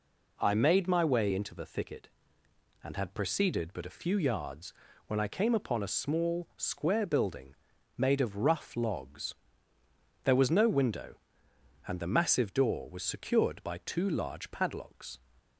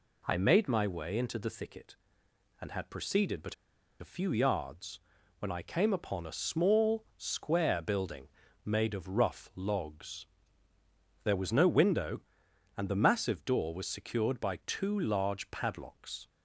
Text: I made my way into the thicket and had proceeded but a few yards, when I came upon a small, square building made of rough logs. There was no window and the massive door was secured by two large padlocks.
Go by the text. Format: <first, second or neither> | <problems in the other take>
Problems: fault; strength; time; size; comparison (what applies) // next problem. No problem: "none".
first | pauses between "but" and "a"; noticeable; at 3.5 s; 0.46 s long // pauses between "building" and "made"; at 8.2 s; 0.38 s long; also in the first